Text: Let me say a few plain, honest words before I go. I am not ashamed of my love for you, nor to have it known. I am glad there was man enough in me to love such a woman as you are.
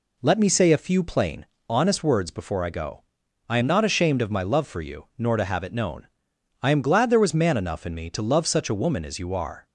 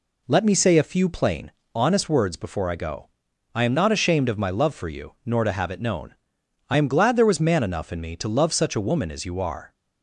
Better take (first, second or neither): neither